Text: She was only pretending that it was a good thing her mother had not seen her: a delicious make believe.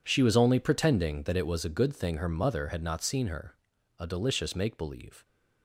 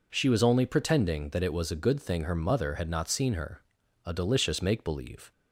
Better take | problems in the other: second | gets quieter; strong; throughout; 15.5 dB

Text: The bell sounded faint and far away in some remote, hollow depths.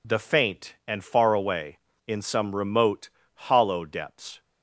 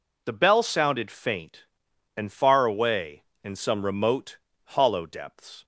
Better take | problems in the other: second | skips "bell sounded"; at 0.1 s

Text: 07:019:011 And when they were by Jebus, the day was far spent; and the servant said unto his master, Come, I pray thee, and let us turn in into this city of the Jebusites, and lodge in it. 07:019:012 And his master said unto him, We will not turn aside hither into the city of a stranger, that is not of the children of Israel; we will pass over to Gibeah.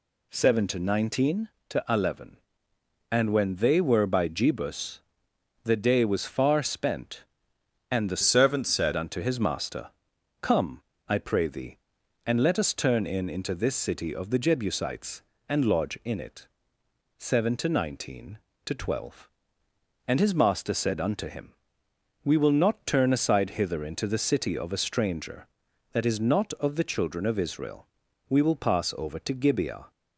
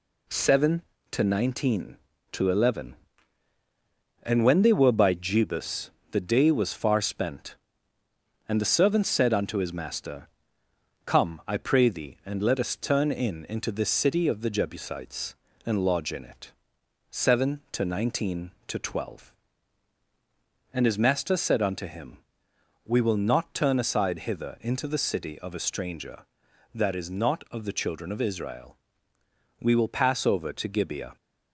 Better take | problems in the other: second | changes voice from "servant" to "said"; from 8.2 to 8.9 s; 0.7 s long

